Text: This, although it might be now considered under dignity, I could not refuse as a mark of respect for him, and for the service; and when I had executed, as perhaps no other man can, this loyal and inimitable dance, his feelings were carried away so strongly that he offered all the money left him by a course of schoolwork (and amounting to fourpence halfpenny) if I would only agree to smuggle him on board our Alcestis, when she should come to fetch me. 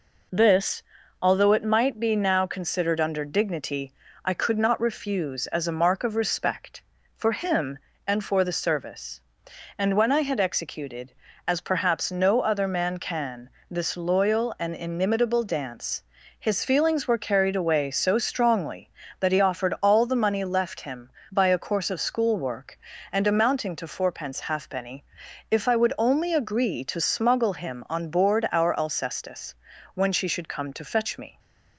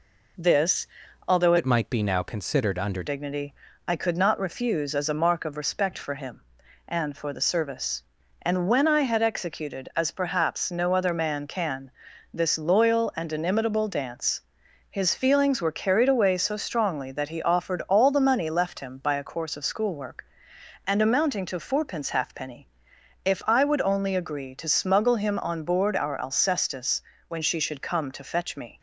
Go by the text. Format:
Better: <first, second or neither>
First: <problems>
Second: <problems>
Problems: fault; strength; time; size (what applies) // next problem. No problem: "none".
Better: first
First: none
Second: changes voice from "it" to "under"; from 1.5 to 3.0 s; 1.5 s long